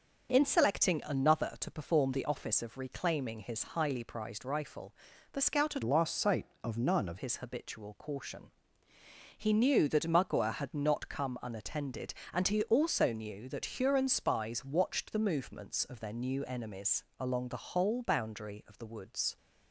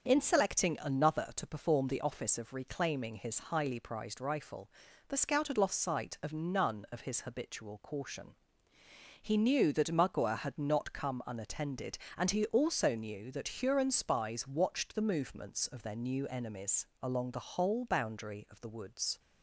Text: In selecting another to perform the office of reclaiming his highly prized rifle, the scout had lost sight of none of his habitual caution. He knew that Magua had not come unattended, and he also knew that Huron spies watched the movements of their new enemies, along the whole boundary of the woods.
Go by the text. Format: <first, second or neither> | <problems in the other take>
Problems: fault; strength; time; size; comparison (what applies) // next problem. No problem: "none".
second | starts louder than the rest; until 1.3 s; 6.5 dB; also in the second // changes voice from "lost" to "of"; from 5.8 to 7.1 s; 1.3 s long